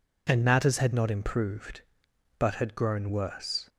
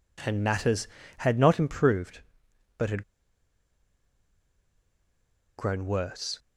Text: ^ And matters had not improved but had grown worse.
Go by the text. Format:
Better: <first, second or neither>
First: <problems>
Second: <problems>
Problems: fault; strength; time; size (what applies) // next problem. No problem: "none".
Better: first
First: none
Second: pauses between "had" and "grown"; strong; at 3.0 s; 2.5 s long